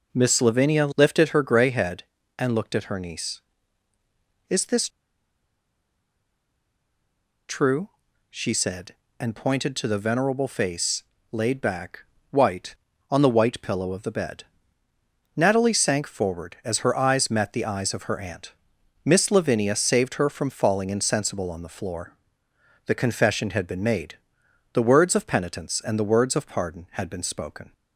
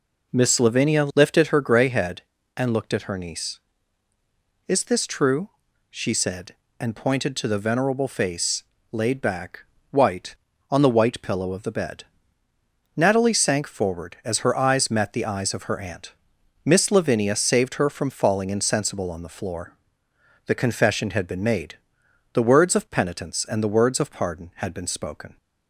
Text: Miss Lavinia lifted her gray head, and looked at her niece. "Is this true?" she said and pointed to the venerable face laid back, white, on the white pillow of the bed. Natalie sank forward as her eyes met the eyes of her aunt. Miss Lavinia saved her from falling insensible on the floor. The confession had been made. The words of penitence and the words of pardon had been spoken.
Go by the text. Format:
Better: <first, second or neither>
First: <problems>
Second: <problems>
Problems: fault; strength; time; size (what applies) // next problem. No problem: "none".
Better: second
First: pauses between "this" and "true"; strong; at 4.8 s; 2.6 s long // pauses between "face" and "laid"; slight; at 11.0 s; 0.30 s long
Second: pauses between "face" and "laid"; slight; at 8.6 s; 0.30 s long